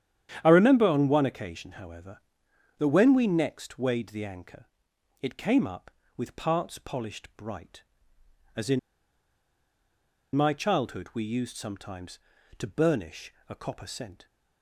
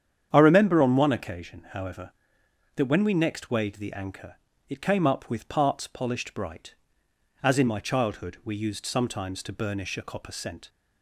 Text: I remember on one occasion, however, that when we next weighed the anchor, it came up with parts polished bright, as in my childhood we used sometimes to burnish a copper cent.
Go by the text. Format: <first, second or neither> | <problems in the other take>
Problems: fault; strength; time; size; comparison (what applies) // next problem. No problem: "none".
second | starts louder than the rest; strong; until 1.4 s; 10 dB; strong in the second // pauses between "in" and "my"; strong; at 8.7 s; 1.5 s long // pauses between "burnish" and "a"; slight; at 13.3 s; 0.16 s long